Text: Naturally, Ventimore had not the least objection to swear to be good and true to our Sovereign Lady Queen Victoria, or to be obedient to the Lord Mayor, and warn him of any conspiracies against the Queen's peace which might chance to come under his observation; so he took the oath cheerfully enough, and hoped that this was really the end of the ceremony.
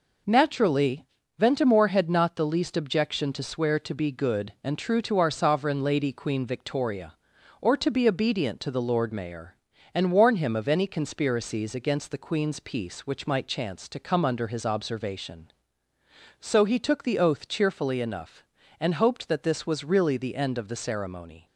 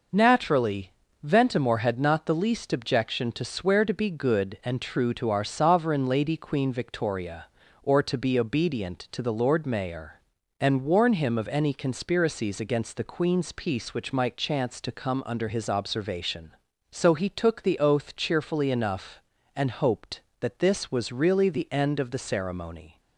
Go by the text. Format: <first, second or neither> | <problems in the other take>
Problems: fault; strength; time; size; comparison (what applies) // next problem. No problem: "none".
neither | none